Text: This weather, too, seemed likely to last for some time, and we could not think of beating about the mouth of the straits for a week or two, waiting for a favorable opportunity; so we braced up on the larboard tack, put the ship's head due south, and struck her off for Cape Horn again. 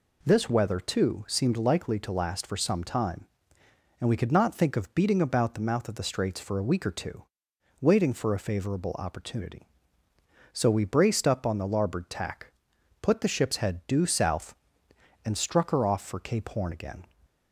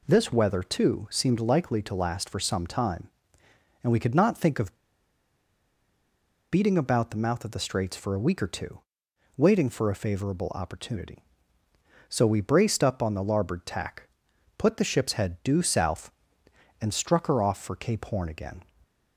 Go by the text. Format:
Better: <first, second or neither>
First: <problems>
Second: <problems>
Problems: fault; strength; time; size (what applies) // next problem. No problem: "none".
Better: first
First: none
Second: pauses between "of" and "beating"; strong; at 4.7 s; 1.7 s long